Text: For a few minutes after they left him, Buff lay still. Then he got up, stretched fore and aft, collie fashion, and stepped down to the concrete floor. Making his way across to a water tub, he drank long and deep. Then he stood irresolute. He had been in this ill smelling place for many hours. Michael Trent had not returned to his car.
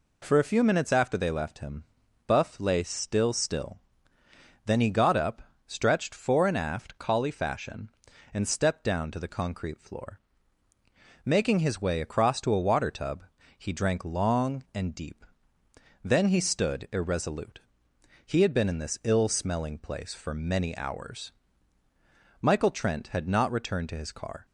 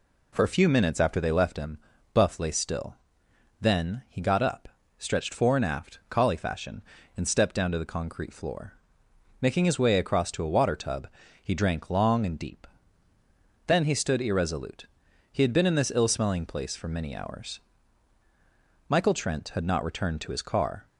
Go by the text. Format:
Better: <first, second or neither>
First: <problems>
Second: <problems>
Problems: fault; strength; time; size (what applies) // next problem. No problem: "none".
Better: second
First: says "still" twice; at 3.3 s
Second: none